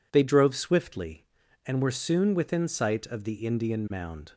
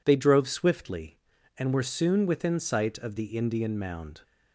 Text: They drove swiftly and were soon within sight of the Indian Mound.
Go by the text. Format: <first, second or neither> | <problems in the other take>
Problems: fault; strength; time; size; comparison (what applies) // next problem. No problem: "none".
neither | none